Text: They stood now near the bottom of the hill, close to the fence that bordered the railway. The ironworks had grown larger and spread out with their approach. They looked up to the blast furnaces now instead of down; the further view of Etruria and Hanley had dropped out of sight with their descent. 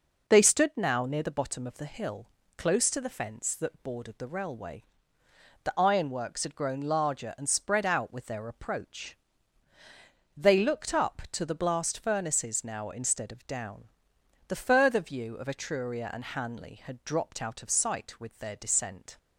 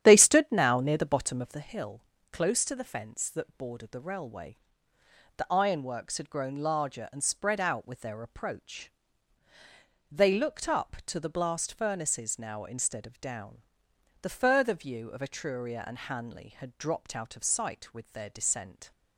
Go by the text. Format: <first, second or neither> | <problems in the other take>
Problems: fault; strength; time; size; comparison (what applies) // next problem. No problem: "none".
first | starts louder than the rest; strong; until 1.6 s; 10.5 dB